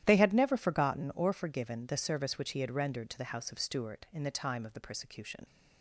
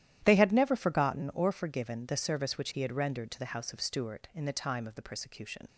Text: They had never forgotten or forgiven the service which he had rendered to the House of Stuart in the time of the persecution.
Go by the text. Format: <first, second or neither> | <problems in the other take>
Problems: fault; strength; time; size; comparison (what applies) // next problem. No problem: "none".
neither | starts louder than the rest; strong; the same in both